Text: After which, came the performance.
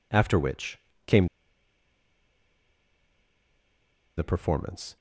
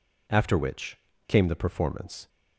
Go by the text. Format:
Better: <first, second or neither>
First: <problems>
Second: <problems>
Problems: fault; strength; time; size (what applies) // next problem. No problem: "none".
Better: second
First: pauses between "came" and "the"; strong; at 1.2 s; 2.9 s long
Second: none